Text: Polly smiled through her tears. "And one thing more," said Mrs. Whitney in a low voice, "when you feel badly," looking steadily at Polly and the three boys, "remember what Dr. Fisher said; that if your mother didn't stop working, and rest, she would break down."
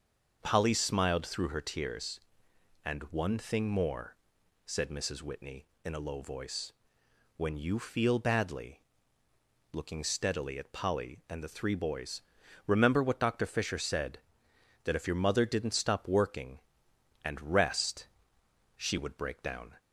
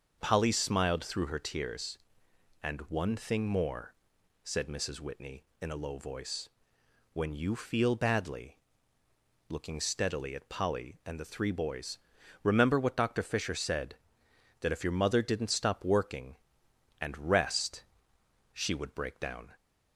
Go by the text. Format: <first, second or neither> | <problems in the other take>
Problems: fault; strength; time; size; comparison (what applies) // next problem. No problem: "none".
neither | starts louder than the rest; the same in both